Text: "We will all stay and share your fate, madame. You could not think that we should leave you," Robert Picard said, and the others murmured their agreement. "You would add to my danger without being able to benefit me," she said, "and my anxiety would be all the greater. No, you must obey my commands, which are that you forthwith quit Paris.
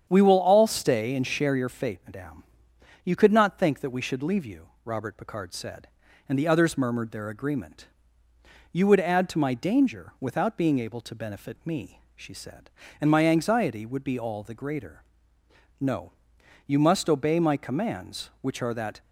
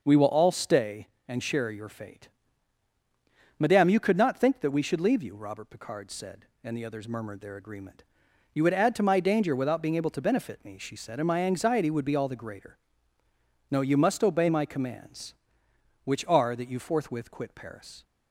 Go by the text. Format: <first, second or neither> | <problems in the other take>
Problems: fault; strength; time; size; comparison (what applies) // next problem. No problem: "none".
second | starts louder than the rest; strong; until 1.1 s; 8.5 dB; also in the second // stops before "you forthwith quit Paris"; at 19.0 s